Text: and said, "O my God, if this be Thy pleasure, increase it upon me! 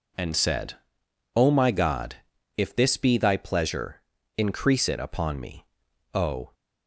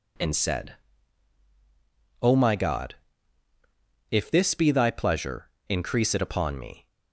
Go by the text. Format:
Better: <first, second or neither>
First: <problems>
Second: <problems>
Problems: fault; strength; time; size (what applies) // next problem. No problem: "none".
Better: second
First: goes on to say "O"; slight; from 6.1 s on; 0.40 s long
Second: none